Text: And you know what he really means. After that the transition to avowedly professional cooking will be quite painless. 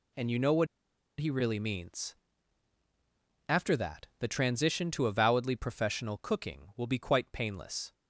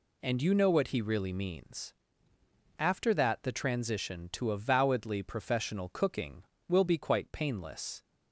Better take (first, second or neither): second